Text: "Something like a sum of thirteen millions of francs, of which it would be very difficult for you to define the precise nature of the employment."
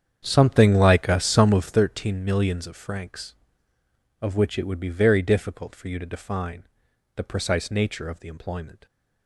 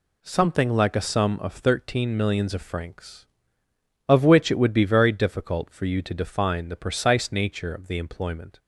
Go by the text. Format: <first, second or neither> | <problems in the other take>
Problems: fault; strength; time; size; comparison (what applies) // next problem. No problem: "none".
second | starts louder than the rest; strong; until 1.8 s; 8.5 dB // pauses between "define" and "the"; noticeable; at 6.6 s; 0.50 s long